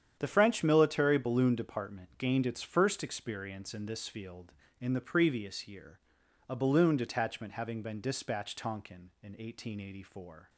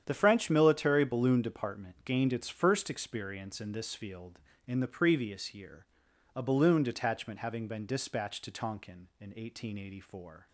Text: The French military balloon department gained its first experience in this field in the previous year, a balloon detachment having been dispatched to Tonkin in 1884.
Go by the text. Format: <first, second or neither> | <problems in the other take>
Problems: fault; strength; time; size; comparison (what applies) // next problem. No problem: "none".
second | starts louder than the rest; strong; until 1.2 s; 9 dB; strong in the second // skips "to"; at 8.5 s